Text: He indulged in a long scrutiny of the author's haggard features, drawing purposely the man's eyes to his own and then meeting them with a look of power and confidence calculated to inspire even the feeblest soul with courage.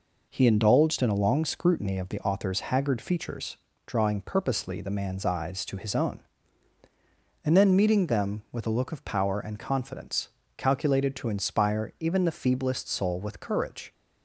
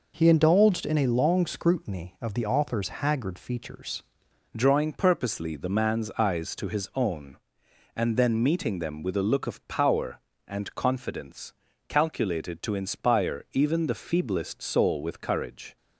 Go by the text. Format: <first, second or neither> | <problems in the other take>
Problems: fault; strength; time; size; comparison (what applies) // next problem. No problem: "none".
first | changes voice at "drawing"; from 4.5 s on; 11.2 s long // pauses between "confidence" and "calculated"; slight; at 11.5 s; 0.36 s long; slight in the first